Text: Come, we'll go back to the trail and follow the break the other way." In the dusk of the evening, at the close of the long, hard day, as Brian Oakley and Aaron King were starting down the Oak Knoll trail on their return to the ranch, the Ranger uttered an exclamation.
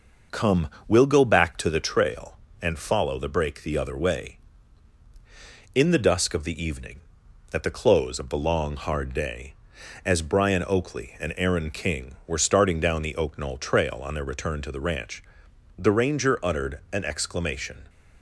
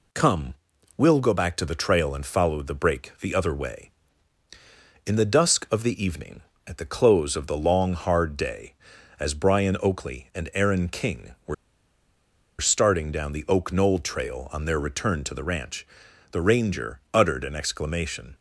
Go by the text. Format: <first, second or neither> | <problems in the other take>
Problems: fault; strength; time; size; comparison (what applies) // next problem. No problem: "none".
first | pauses between "were" and "starting"; at 11.5 s; 1.0 s long